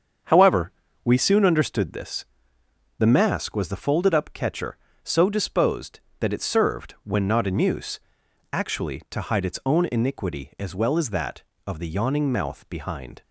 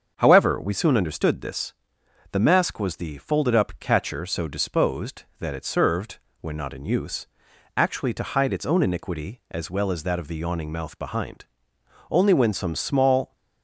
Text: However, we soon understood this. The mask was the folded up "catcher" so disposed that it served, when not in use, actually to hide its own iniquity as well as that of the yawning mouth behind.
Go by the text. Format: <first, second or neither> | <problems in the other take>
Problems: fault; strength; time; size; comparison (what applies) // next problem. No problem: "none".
first | starts louder than the rest; until 1.1 s; 7 dB; strong in the first // goes on to say "Only when some small"; noticeable; from 12.1 s on; 1.2 s long